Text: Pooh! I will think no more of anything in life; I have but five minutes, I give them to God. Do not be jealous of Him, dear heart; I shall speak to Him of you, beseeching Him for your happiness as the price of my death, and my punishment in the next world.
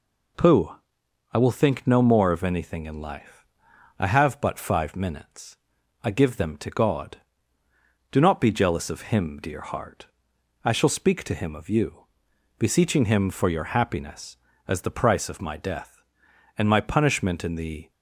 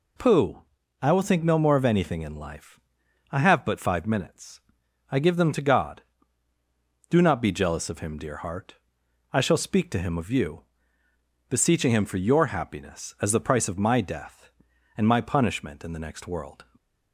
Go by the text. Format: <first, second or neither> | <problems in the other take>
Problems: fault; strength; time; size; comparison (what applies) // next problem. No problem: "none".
second | stops before "next world"; at 17.9 s